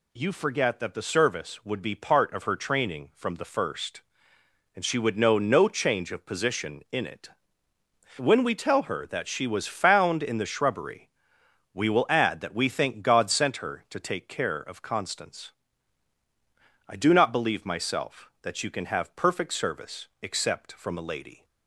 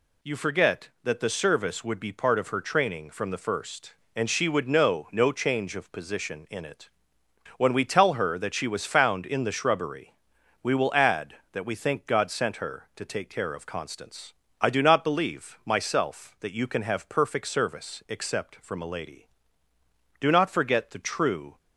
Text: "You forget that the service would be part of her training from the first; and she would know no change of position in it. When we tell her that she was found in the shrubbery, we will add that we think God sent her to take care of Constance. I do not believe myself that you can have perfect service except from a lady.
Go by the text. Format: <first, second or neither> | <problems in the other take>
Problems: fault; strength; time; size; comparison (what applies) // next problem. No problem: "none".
first | goes on to say "Do not forget the true"; from 20.1 s on; 1.4 s long